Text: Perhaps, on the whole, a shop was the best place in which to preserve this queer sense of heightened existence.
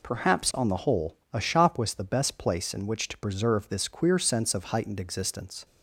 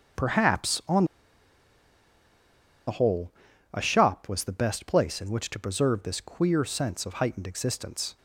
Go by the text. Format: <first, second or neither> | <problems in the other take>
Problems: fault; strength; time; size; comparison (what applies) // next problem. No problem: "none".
first | starts louder than the rest; until 3.0 s; 7 dB // pauses between "on" and "the"; strong; at 1.0 s; 1.8 s long